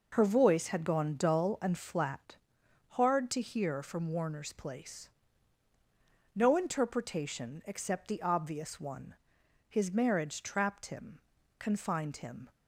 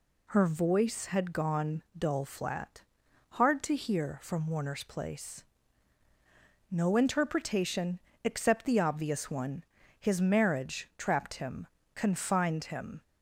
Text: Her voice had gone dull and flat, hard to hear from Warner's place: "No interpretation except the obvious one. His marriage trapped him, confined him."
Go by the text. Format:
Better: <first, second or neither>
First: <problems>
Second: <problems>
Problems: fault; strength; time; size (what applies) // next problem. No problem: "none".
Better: first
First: none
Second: skips "and"; at 2.2 s // pauses between "interpretation" and "except"; slight; at 8.0 s; 0.24 s long